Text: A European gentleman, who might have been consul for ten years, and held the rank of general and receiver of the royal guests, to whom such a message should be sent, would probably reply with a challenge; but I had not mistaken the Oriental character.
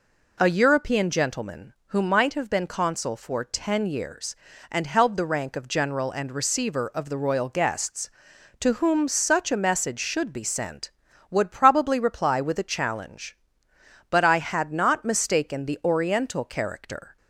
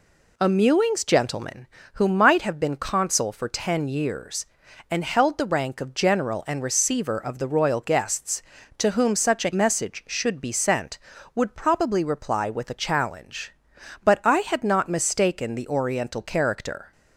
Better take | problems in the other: first | says "Mewings" for "European"; at 0.4 s

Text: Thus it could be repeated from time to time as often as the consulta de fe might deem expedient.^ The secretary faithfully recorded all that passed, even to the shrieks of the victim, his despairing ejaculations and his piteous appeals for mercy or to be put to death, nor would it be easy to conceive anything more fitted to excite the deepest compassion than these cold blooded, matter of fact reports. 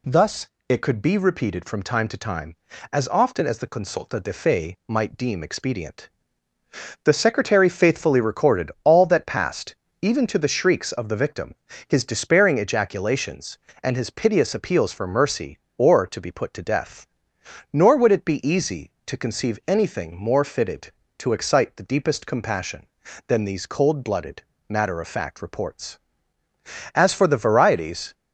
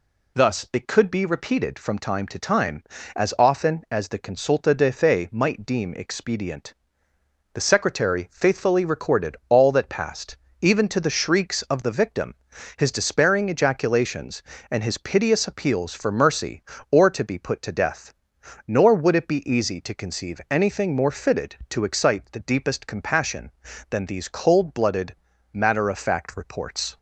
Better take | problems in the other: second | pauses between "Thus" and "it"; slight; at 0.4 s; 0.24 s long // goes on to say "As for the varieties"; noticeable; from 26.9 s on; 1.2 s long

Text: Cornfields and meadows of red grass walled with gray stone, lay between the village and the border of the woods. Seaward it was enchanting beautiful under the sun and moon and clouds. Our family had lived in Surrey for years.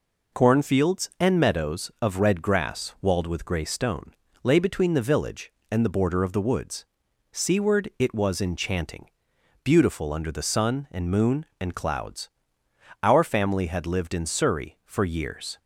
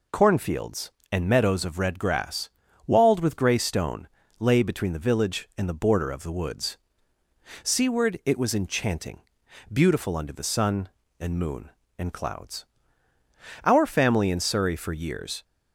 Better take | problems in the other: first | pauses between "grass" and "walled"; at 2.4 s; 0.38 s long // pauses between "enchanting" and "beautiful"; noticeable; at 9.2 s; 0.52 s long; noticeable in the first // skips "had lived"; at 14.2 s

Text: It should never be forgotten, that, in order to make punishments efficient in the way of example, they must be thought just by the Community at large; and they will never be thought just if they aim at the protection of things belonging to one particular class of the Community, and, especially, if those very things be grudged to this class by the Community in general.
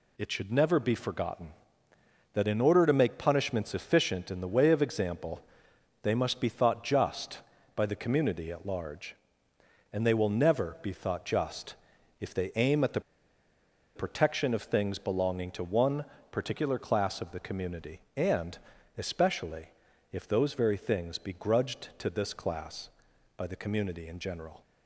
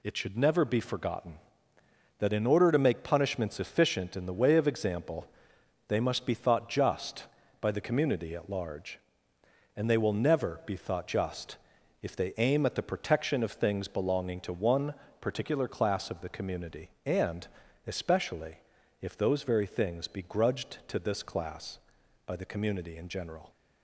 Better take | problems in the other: second | pauses between "just" and "if"; at 11.7 s; 0.44 s long; also in the second // pauses between "the" and "protection"; noticeable; at 13.0 s; 0.95 s long // pauses between "one" and "particular"; slight; at 16.0 s; 0.26 s long; slight in the second

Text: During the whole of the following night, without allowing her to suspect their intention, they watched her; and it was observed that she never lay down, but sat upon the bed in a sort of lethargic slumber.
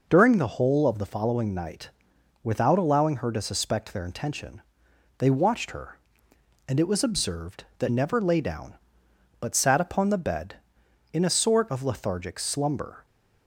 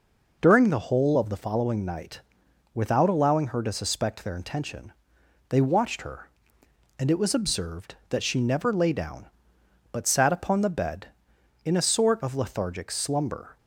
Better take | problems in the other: second | skips "she"; at 7.8 s

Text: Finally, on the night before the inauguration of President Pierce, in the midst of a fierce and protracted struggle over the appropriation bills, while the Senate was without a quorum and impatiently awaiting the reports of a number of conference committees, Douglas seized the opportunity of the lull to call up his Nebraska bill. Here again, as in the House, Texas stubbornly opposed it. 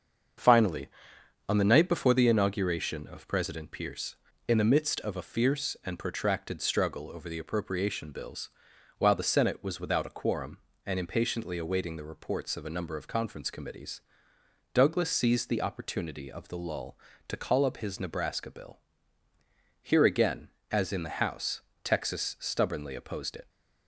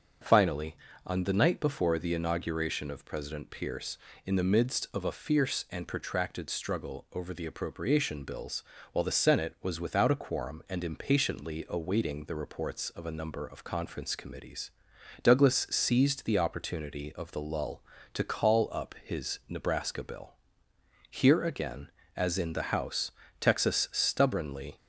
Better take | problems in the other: first | starts louder than the rest; until 1.5 s; 7 dB; also in the first // stops before "opposed it"; at 24.7 s

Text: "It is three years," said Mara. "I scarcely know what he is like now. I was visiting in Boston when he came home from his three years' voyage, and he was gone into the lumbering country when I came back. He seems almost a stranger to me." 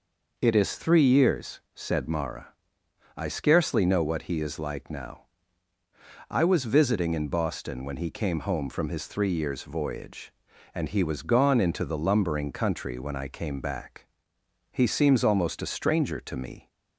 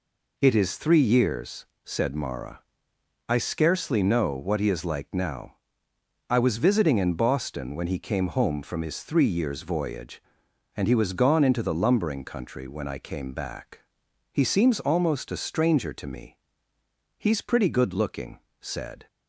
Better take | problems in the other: first | goes on to say "He's pretty good looking said"; strong; from 17.1 s on; 1.9 s long

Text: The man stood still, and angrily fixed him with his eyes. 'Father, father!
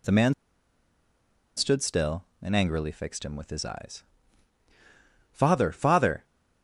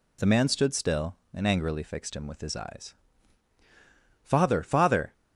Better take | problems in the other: second | pauses between "man" and "stood"; at 0.3 s; 1.2 s long

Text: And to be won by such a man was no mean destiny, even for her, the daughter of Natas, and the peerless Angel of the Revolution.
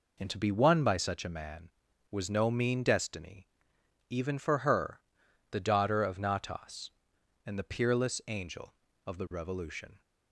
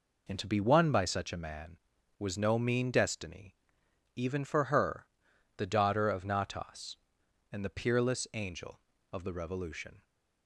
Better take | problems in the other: neither | none

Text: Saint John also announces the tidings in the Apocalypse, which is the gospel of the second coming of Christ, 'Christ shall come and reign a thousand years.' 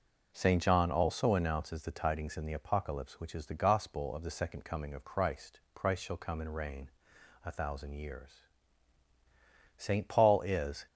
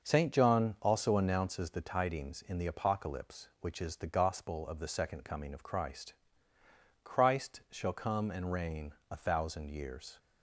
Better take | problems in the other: second | pauses between "reign" and "a"; noticeable; at 6.8 s; 0.56 s long; slight in the second // goes on to say "Saint Paul is"; noticeable; from 9.7 s on; 1.1 s long

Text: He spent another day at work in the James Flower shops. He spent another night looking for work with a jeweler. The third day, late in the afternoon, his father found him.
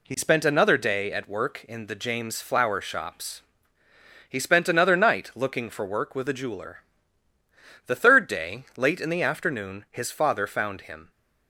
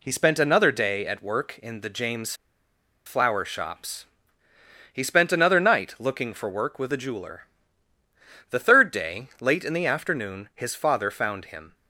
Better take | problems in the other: first | pauses between "James" and "Flower"; noticeable; at 2.3 s; 0.71 s long

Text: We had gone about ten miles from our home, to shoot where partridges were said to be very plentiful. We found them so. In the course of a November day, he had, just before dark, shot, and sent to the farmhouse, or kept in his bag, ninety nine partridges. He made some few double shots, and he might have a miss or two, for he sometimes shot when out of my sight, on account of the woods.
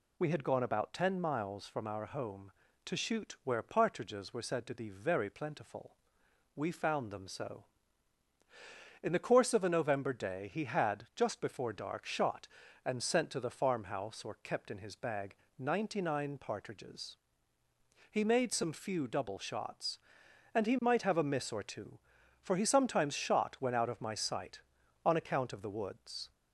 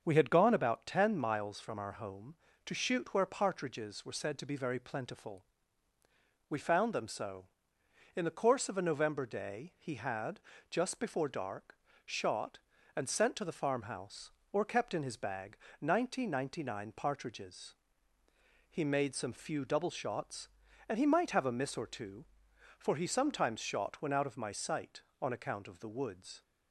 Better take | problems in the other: first | starts louder than the rest; until 1.0 s; 7 dB // says "ninety" twice; at 16.2 s

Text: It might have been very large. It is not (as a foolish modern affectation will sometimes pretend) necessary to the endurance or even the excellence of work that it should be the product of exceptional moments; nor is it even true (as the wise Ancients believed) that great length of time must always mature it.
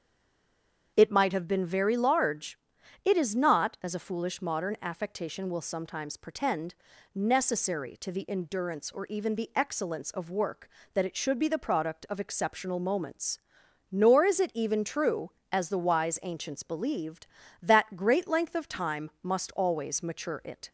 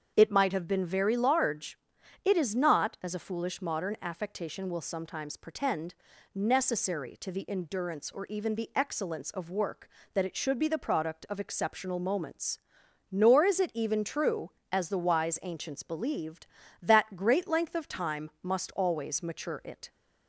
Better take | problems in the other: second | stays silent before the first word; slight; until 0.9 s; 0.9 s long // starts louder than the rest; strong; until 1.9 s; 7 dB; strong in the second

